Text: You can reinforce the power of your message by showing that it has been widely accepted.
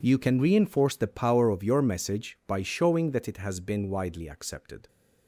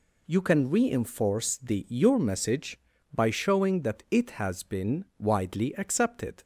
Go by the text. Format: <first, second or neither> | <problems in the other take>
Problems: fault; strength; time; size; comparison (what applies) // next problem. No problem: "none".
first | skips "power of"; at 1.8 s